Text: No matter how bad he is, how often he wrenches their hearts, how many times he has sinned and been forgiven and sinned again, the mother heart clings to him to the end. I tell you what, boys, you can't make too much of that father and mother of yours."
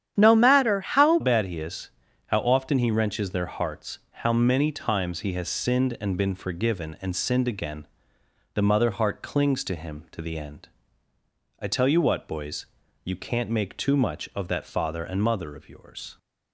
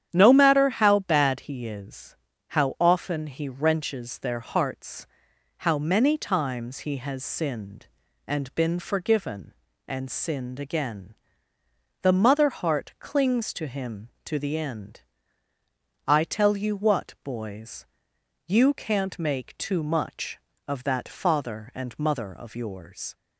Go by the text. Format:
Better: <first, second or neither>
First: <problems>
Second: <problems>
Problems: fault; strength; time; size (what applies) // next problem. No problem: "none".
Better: second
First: starts louder than the rest; strong; until 1.1 s; 10 dB // changes voice at "bad"; from 1.2 s on; 14.9 s long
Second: starts louder than the rest; strong; until 1.1 s; 9.5 dB